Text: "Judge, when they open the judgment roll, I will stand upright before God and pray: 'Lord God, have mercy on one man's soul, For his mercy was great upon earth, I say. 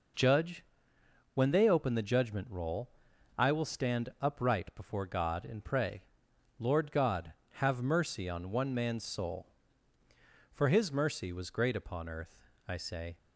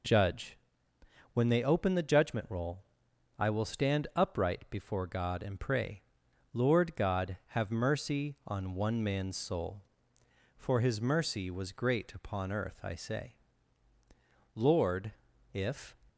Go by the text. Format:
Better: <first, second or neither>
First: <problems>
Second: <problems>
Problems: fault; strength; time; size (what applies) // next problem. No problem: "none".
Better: first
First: none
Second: goes on to say "Lord if"; from 14.5 s on; 1.4 s long